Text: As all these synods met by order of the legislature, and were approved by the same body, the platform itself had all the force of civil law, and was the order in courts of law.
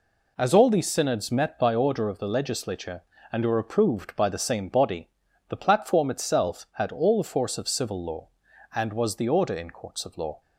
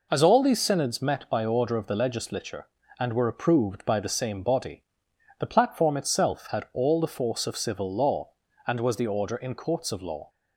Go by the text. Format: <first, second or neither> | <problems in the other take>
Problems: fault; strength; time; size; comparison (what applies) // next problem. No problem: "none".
neither | none